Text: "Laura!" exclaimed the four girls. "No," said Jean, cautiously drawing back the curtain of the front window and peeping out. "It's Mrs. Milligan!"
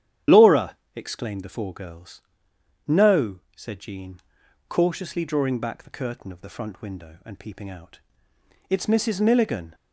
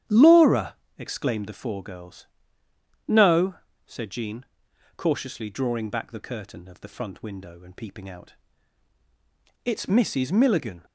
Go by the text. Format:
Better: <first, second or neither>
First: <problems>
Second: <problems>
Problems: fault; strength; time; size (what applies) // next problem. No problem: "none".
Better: second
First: loses the start of "Laura"; at 0.2 s; 30 ms // starts louder than the rest; strong; until 1.4 s; 10 dB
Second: starts louder than the rest; strong; until 1.3 s; 10.5 dB